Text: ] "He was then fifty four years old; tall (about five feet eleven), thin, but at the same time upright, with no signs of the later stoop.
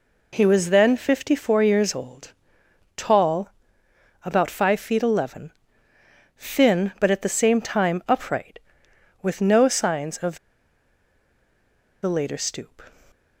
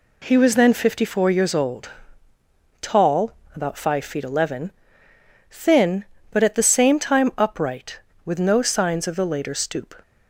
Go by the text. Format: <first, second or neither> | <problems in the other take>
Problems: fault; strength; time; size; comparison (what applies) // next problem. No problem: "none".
second | pauses between "of" and "the"; strong; at 10.3 s; 1.6 s long